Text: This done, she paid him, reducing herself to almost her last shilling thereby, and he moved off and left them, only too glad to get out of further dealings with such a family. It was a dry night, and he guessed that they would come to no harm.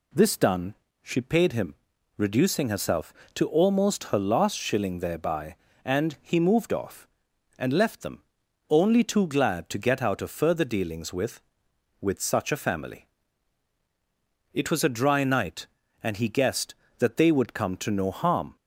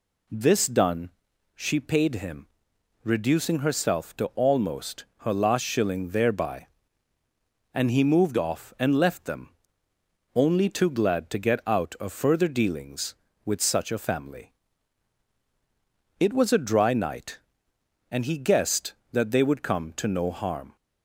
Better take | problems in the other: second | says "with" twice; at 12.0 s

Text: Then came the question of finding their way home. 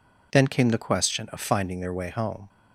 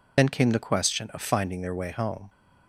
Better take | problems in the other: first | loses the start of "Then"; at 0.1 s; 40 ms

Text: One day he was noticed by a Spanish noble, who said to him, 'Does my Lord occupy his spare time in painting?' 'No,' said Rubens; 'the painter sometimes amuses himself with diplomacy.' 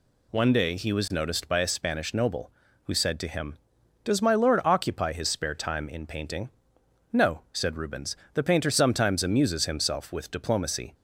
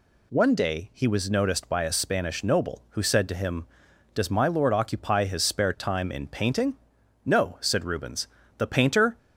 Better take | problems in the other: first | stops before "sometimes amuses himself with diplomacy"; at 9.1 s

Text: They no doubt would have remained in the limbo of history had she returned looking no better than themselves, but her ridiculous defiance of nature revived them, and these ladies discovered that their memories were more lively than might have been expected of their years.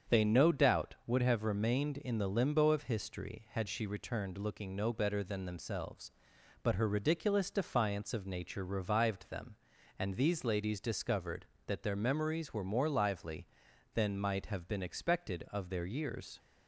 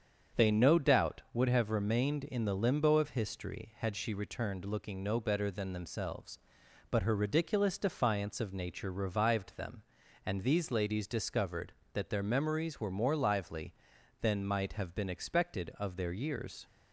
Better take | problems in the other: neither | starts louder than the rest; strong; the same in both

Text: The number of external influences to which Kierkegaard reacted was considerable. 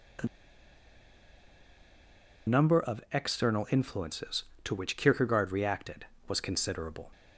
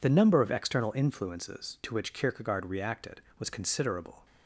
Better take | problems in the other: second | pauses between "The" and "number"; strong; at 0.2 s; 2.1 s long

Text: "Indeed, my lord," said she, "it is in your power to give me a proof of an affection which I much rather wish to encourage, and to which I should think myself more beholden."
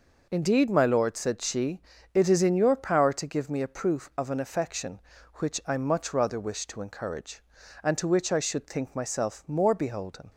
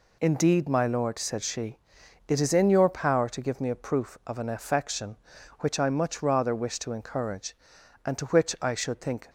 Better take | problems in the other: first | stops before "myself more beholden"; at 9.2 s

